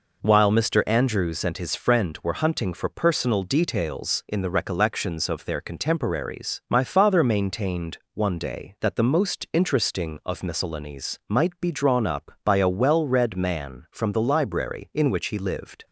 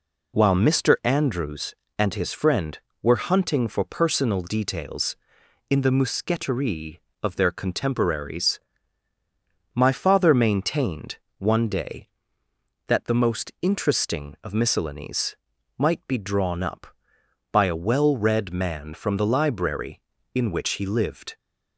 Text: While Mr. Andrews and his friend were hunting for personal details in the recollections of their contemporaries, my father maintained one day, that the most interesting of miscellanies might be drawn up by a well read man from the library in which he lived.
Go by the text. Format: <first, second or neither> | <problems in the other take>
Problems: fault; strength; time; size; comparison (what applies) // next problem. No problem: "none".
first | says "mousqueterie" for "recollections"; at 5.9 s // pauses between "maintained" and "one"; slight; at 11.1 s; 0.20 s long; slight in the first // pauses between "miscellanies" and "might"; at 15.3 s; 0.42 s long